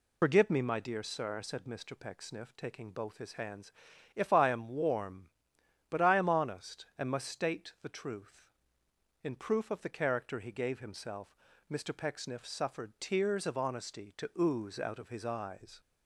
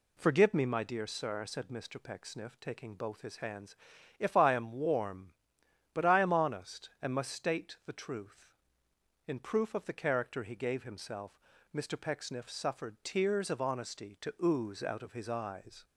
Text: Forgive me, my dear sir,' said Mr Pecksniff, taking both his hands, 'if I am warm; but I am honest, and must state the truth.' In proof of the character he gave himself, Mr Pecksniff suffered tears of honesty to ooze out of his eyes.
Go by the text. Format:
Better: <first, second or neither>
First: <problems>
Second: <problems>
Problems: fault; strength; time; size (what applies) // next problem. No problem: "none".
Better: second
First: loses the start of "Forgive"; at 0.2 s; 80 ms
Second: none